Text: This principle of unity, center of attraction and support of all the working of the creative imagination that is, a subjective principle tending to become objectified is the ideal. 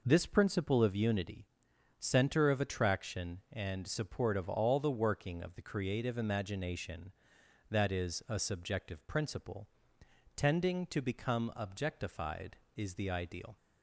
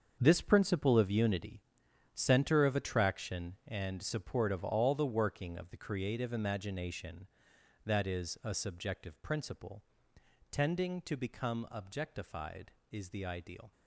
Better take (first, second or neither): first